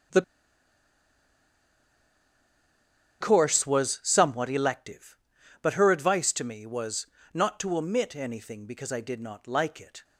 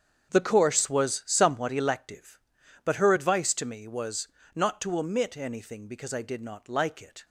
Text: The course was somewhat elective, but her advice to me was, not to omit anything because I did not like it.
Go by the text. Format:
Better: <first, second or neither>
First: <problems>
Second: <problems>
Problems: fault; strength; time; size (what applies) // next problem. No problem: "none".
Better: second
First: starts louder than the rest; strong; until 4.1 s; 7.5 dB // pauses between "The" and "course"; strong; at 0.2 s; 2.9 s long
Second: starts louder than the rest; strong; until 1.3 s; 7.5 dB